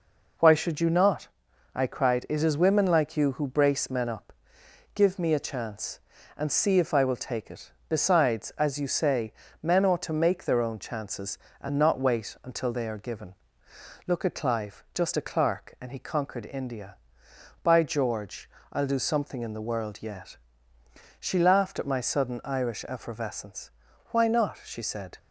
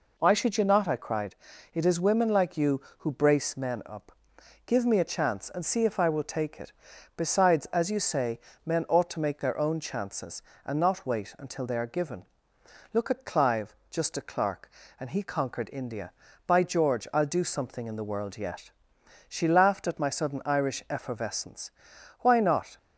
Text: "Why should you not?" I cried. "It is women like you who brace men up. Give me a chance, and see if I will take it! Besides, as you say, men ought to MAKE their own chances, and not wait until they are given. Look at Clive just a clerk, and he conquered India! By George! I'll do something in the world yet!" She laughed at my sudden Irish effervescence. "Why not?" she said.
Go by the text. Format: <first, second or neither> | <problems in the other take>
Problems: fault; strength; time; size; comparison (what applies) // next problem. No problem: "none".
first | stops before "she said"; at 22.7 s